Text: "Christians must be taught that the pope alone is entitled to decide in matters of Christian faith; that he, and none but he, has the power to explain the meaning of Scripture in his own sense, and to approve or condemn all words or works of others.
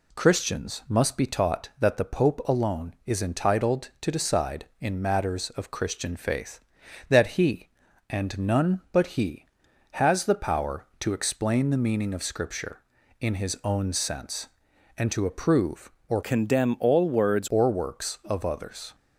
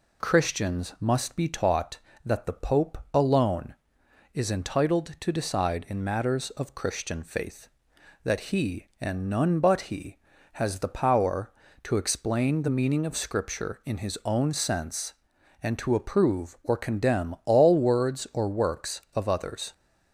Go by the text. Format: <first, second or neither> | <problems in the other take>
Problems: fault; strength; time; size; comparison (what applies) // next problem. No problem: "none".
second | changes voice from "condemn" to "words"; from 16.2 to 17.4 s; 1.2 s long